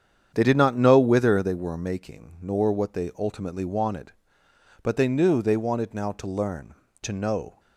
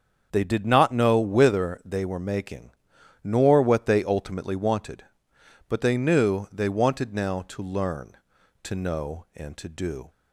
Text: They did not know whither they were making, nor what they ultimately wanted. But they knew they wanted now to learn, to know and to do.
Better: second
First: starts louder than the rest; strong; until 1.3 s; 8 dB // stops before "and to do"; at 7.5 s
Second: starts louder than the rest; until 1.3 s; 7 dB

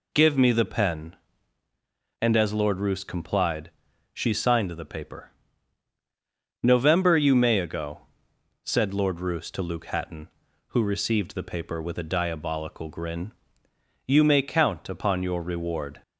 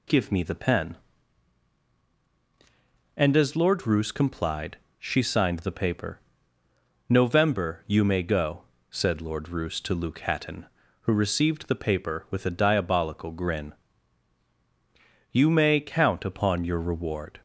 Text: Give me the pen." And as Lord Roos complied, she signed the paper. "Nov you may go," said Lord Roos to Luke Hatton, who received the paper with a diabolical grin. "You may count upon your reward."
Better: second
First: says "ago" for "go"; at 7.5 s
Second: none

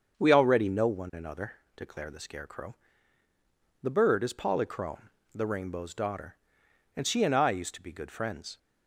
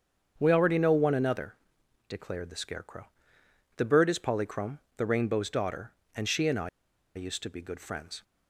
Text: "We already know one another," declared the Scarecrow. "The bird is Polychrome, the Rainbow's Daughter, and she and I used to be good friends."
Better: first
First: starts louder than the rest; until 1.2 s; 7 dB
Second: starts louder than the rest; strong; until 1.3 s; 7.5 dB // pauses between "I" and "used"; noticeable; at 6.6 s; 0.46 s long

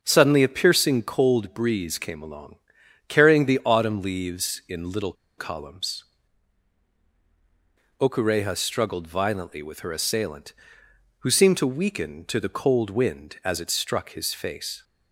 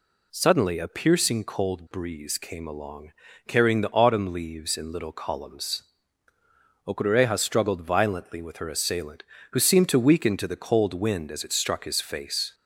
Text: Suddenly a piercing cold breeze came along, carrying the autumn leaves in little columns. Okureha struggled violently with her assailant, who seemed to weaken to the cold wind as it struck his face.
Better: second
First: starts louder than the rest; until 1.0 s; 6.5 dB // pauses between "little" and "columns"; slight; at 5.1 s; 0.24 s long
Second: none

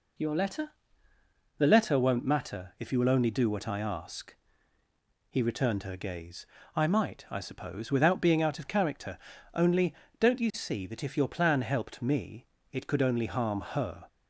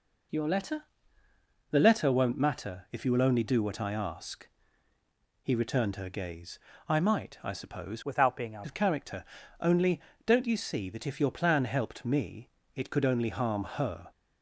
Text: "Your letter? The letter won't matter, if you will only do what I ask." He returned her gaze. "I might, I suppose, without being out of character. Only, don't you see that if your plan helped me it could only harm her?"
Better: first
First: pauses between "me" and "it"; slight; at 12.4 s; 0.24 s long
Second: changes voice from "without" to "out"; from 8.0 to 8.6 s; 0.6 s long // pauses between "me" and "it"; slight; at 12.4 s; 0.24 s long

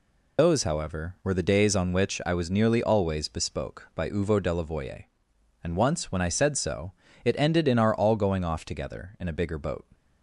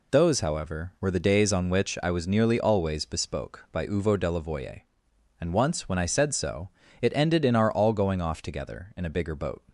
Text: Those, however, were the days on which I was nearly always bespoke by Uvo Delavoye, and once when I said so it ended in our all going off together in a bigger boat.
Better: second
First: loses the start of "Those"; at 0.3 s; 40 ms // pauses between "so" and "it"; slight; at 6.9 s; 0.32 s long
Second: pauses between "so" and "it"; slight; at 6.6 s; 0.32 s long

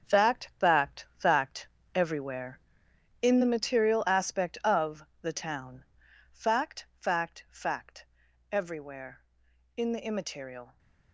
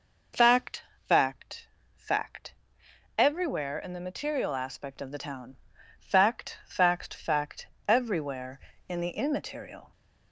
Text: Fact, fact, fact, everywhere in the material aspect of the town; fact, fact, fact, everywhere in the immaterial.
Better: second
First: gets quieter; strong; throughout; 9 dB // pauses between "of" and "the"; slight; at 5.0 s; 0.20 s long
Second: none

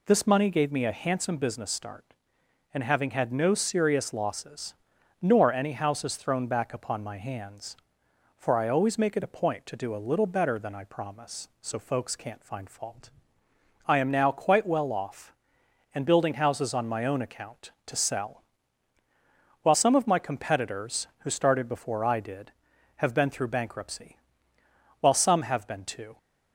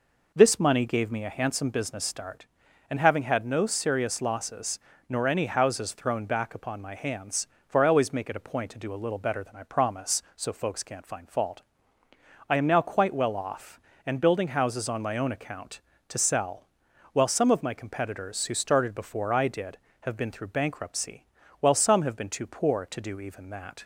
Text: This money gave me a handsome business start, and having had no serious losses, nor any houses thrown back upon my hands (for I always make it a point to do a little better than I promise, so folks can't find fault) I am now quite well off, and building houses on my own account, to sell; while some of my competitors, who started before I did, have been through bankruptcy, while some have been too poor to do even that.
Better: second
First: stops before "poor to do even that"; at 26.1 s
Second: none

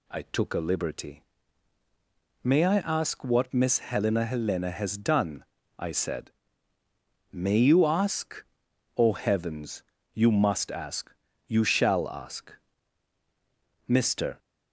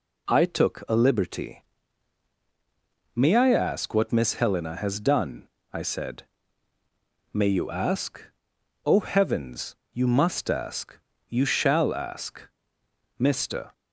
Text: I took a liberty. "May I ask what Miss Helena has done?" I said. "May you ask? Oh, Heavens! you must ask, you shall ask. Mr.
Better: second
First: says "Helena" twice; at 4.2 s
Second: none

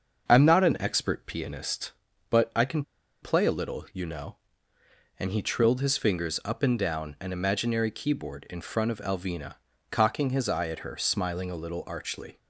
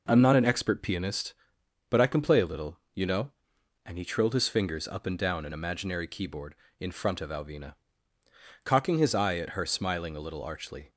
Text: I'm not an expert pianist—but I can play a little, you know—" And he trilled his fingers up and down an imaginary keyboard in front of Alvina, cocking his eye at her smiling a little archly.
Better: second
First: starts louder than the rest; until 1.3 s; 6.5 dB // pauses between "can" and "play"; at 2.8 s; 0.40 s long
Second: none

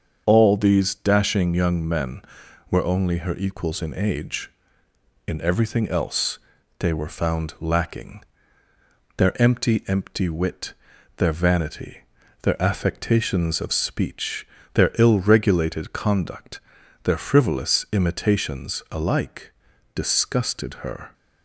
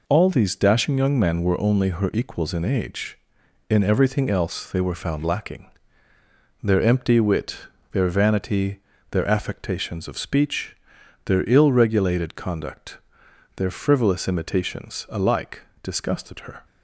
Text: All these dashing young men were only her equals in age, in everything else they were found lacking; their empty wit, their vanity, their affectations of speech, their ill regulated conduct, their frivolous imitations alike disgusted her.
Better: second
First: starts louder than the rest; until 1.2 s; 7 dB // pauses between "else" and "they"; at 6.3 s; 0.40 s long // says "empty" twice; at 9.8 s // pauses between "alike" and "disgusted"; at 19.5 s; 0.42 s long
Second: pauses between "alike" and "disgusted"; slight; at 15.6 s; 0.18 s long

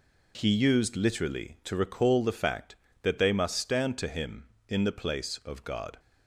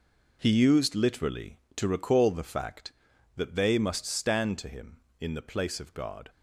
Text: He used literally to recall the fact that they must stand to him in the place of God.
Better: neither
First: none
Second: none

